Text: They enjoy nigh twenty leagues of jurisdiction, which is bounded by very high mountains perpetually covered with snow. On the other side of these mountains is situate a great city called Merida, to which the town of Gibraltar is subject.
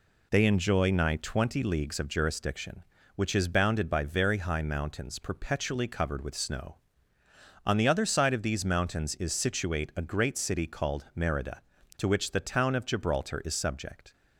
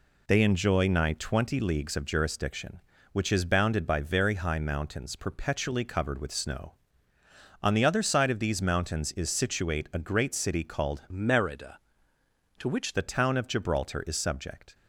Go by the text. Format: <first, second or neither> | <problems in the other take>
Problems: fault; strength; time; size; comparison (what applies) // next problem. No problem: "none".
first | changes voice from "Merida" to "which"; from 11.1 to 12.9 s; 1.8 s long